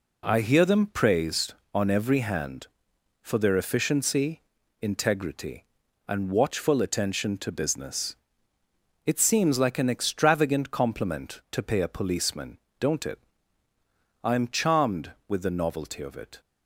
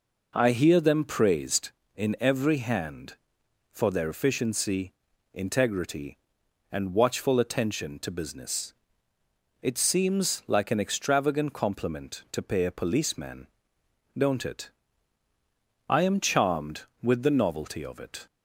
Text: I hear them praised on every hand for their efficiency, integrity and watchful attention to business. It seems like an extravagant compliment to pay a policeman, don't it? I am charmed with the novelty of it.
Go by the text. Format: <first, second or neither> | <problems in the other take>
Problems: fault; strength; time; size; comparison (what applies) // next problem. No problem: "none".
first | says "in" for "on"; at 1.9 s